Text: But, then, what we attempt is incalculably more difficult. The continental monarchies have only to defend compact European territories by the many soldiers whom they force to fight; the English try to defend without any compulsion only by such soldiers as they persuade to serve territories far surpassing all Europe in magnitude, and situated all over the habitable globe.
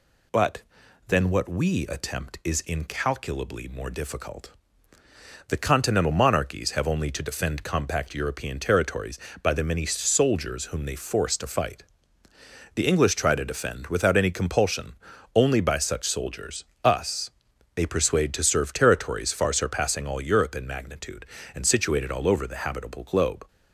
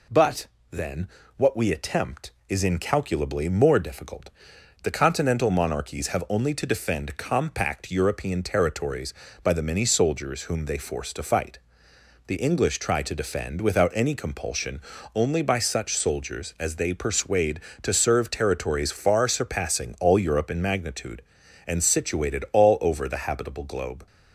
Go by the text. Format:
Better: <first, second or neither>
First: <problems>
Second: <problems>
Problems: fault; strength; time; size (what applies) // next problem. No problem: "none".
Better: second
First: pauses between "compulsion" and "only"; at 14.9 s; 0.38 s long // says "us" for "as"; at 16.8 s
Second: pauses between "compulsion" and "only"; slight; at 14.7 s; 0.36 s long